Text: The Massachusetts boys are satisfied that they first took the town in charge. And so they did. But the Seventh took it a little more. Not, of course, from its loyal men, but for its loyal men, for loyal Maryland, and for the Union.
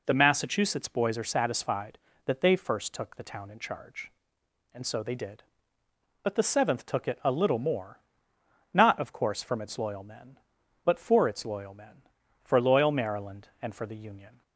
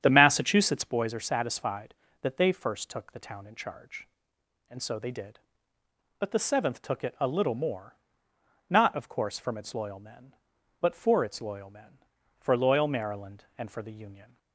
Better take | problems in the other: first | starts louder than the rest; strong; until 1.0 s; 9 dB

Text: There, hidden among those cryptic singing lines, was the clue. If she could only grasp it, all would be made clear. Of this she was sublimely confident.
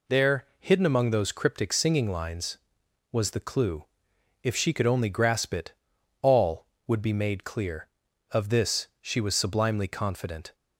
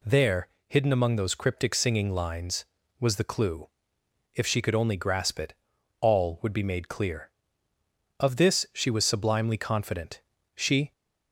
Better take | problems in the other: first | goes on to say "She"; slight; from 10.5 s on; 0.36 s long

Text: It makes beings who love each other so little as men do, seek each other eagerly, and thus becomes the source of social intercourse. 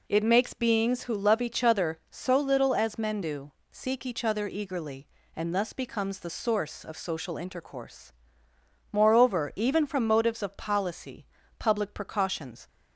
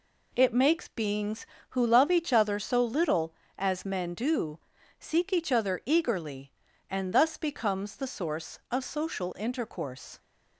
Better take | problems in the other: second | goes on to say "Moreover even from motives of policy public precautions"; strong; from 8.9 s on; 3.7 s long

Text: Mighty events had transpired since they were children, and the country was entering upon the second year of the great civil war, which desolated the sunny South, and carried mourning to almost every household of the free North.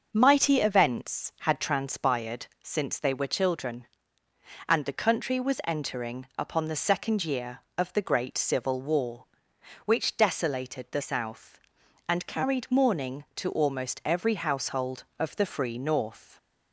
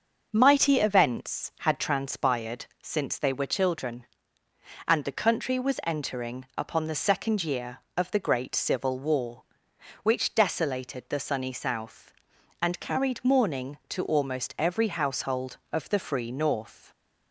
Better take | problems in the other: second | starts louder than the rest; until 1.1 s; 6 dB; also in the second // pauses between "transpired" and "since"; slight; at 2.4 s; 0.16 s long; slight in the second // skips "sunny"; at 11.0 s

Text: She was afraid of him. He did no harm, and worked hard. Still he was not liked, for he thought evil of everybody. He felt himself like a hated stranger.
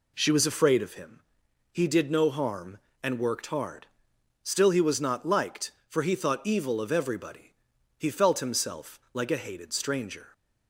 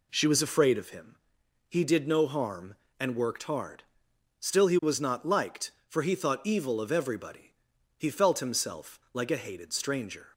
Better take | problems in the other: neither | none

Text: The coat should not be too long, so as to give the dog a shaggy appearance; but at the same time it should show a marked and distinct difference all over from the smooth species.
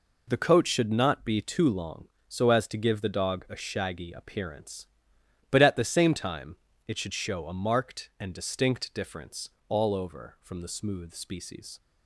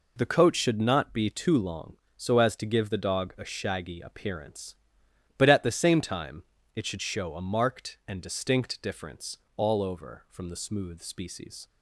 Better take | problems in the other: neither | pauses between "time" and "it"; slight; the same in both // pauses between "difference" and "all"; slight; the same in both

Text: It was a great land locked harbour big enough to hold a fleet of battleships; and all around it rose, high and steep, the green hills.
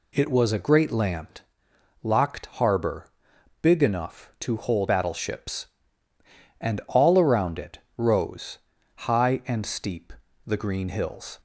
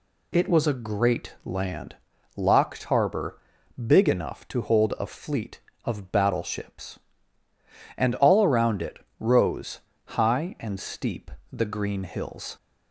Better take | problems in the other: second | pauses between "land" and "locked"; noticeable; at 1.3 s; 0.64 s long; also in the second // pauses between "harbour" and "big"; noticeable; at 3.0 s; 0.52 s long; noticeable in the second // skips "a fleet of"; at 4.8 s // pauses between "it" and "rose"; slight; at 7.8 s; 0.16 s long; slight in the second

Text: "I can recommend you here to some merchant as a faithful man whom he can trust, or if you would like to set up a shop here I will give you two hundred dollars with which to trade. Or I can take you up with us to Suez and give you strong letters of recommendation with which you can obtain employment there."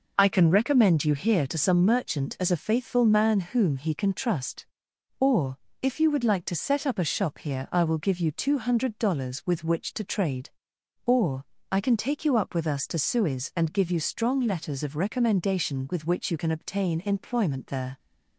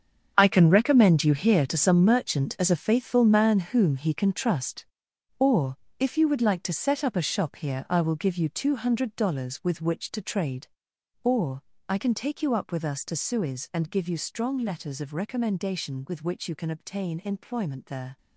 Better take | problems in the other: first | gets quieter; strong; throughout; 12.5 dB // pauses between "or" and "if"; slight; at 5.7 s; 0.22 s long; slight in the first // pauses between "Or" and "I"; slight; at 11.6 s; 0.26 s long; slight in the first

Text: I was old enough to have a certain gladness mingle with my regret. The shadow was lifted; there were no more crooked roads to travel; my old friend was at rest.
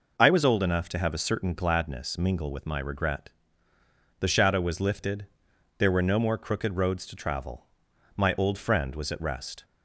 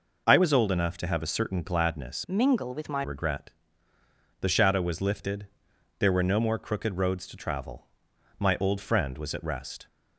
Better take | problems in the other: first | changes voice from "mingle" to "my"; from 2.2 to 3.0 s; 0.8 s long

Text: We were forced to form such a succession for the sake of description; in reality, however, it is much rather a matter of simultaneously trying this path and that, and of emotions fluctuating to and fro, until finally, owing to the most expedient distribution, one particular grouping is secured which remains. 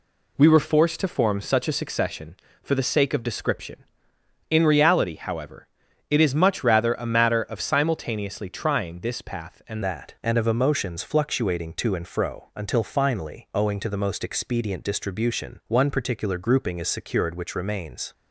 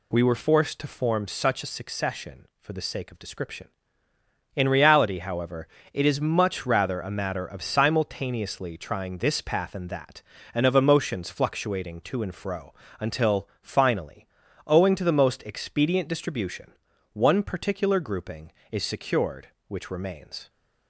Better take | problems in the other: second | changes voice at "that"; from 9.8 s on; 8.3 s long

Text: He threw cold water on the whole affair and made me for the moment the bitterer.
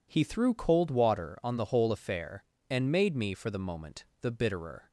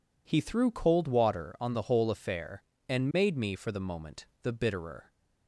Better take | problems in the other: neither | pauses between "moment" and "the"; slight; the same in both

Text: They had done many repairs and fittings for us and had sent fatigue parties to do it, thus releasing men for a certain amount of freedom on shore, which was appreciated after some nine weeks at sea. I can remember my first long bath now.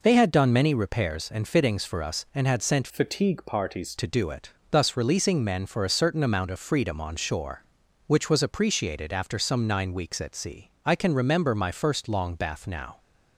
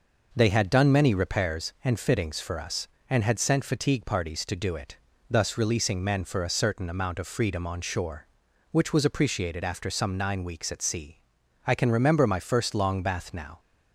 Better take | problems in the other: second | changes voice from "fatigue" to "parties"; from 2.9 to 3.9 s; 1.0 s long

